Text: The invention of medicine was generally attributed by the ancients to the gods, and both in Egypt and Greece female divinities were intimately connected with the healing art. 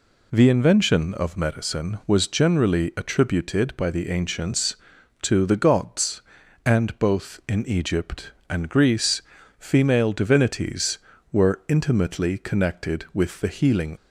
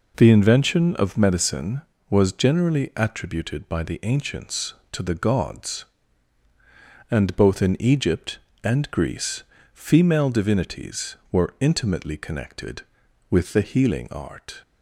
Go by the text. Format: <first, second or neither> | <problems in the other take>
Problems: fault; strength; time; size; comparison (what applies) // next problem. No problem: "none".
second | pauses between "Greece" and "female"; at 9.2 s; 0.38 s long; slight in the second // stops before "art"; at 13.9 s